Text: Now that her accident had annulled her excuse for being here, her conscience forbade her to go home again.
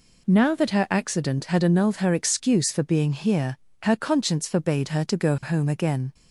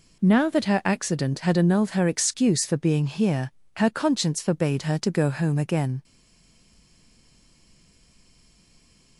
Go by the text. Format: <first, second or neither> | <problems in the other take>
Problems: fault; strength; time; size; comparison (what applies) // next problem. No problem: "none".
first | stays silent after the last word; strong; from 6.0 s on; 3.1 s long